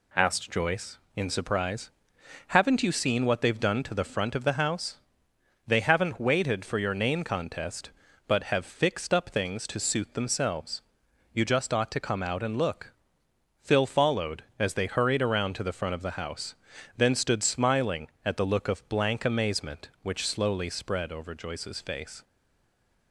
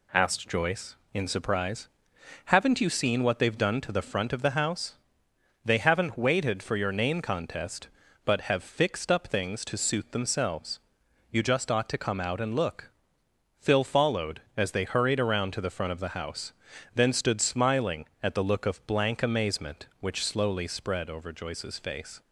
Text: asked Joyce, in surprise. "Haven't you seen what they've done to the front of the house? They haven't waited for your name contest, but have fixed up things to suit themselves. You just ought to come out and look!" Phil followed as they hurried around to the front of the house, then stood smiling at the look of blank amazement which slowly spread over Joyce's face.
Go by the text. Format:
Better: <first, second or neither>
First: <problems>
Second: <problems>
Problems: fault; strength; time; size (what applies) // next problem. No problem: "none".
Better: second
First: stays silent after the last word; slight; from 22.2 s on; 0.9 s long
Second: none